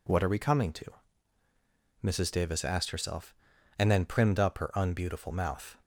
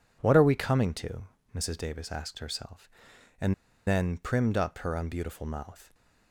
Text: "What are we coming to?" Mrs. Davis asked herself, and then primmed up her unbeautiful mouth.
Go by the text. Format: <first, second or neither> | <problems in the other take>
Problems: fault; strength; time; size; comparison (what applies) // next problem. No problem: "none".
first | pauses between "and" and "then"; slight; at 3.5 s; 0.33 s long